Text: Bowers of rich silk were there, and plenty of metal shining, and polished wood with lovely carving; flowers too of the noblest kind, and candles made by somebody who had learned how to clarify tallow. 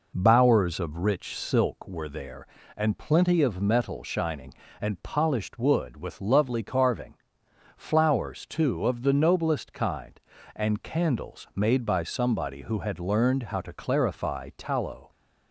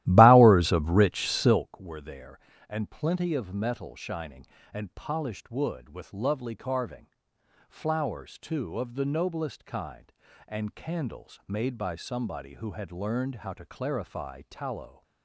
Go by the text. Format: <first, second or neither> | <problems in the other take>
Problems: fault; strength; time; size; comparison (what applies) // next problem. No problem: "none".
first | starts louder than the rest; strong; until 1.7 s; 15 dB